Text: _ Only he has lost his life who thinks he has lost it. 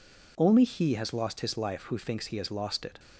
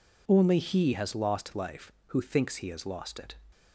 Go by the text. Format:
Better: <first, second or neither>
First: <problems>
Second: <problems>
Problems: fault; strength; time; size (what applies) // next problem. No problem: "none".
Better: first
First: none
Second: skips "his"; at 1.5 s